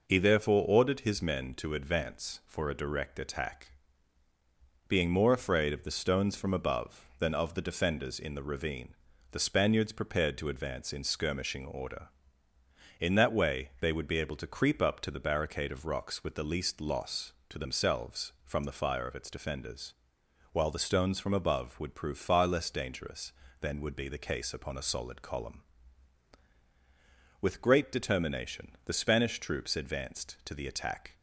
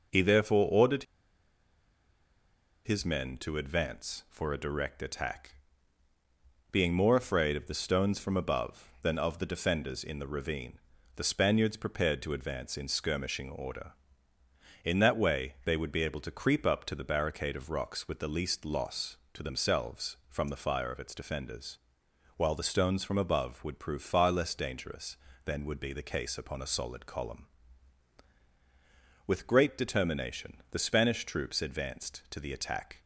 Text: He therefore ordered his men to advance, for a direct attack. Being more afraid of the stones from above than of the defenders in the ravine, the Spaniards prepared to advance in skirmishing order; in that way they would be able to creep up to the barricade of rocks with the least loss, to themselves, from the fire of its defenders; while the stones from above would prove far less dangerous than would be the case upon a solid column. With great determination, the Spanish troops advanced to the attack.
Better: first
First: none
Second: pauses between "ordered" and "his"; strong; at 1.0 s; 1.8 s long

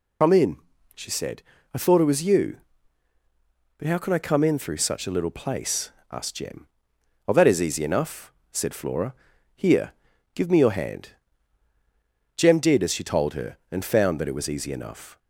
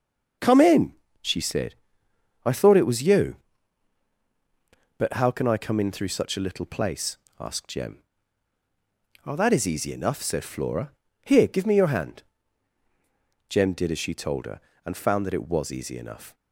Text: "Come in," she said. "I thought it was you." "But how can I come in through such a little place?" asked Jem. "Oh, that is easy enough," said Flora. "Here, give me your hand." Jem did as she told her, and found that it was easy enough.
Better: second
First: loses the start of "Come"; at 0.2 s; 105 ms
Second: none

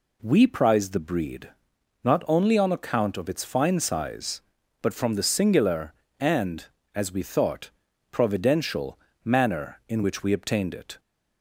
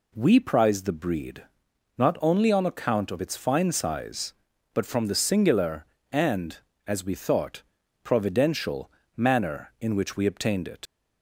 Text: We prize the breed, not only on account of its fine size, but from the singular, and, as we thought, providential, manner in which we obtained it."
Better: first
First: none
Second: leaves "it" unfinished; at 10.8 s; 70 ms

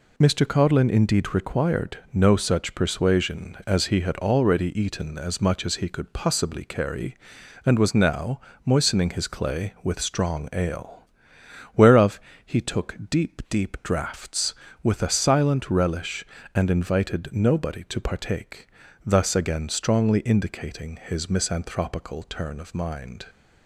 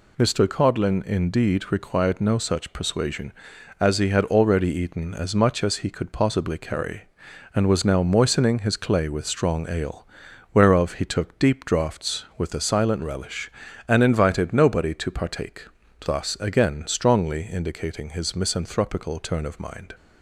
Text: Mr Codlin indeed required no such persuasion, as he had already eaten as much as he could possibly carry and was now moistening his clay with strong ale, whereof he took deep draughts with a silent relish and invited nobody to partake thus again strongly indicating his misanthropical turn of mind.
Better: second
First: pauses between "now" and "moistening"; slight; at 8.3 s; 0.26 s long // pauses between "whereof" and "he"; slight; at 12.2 s; 0.24 s long // says "deep" twice; at 13.4 s // pauses between "partake" and "thus"; slight; at 18.6 s; 0.36 s long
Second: pauses between "partake" and "thus"; at 15.6 s; 0.40 s long

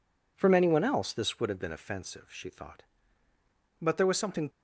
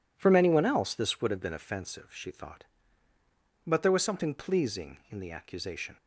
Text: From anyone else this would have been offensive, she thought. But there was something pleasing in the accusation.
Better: second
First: stops before "pleasing in the accusation"; at 4.4 s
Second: none

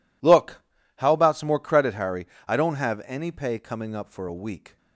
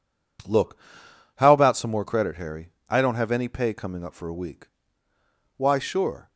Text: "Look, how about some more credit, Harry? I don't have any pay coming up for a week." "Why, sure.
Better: second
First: stops before "Why sure"; at 4.7 s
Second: none

